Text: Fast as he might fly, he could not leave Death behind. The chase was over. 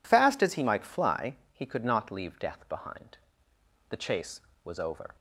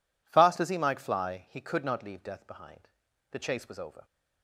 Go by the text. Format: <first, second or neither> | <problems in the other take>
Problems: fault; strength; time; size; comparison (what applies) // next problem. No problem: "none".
neither | none